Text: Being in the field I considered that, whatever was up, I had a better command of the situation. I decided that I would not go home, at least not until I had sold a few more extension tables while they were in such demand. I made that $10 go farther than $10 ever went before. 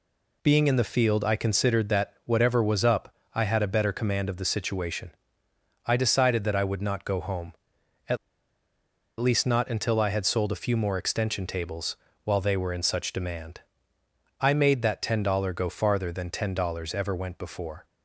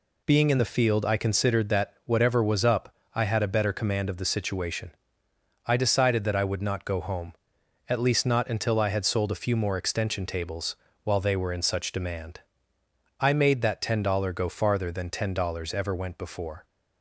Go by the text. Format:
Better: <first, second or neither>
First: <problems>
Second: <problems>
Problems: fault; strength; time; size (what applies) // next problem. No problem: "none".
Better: second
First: pauses between "at" and "least"; at 8.1 s; 1.0 s long // pauses between "tables" and "while"; slight; at 11.9 s; 0.28 s long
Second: pauses between "tables" and "while"; slight; at 10.7 s; 0.28 s long